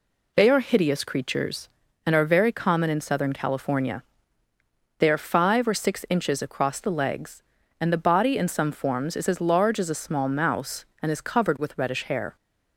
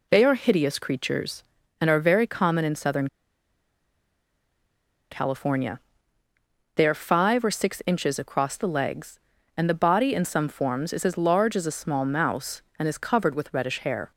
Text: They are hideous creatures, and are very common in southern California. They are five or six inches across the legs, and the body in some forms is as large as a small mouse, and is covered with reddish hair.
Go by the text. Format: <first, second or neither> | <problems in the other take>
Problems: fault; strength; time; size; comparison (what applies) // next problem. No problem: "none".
first | pauses between "southern" and "California"; strong; at 3.0 s; 2.0 s long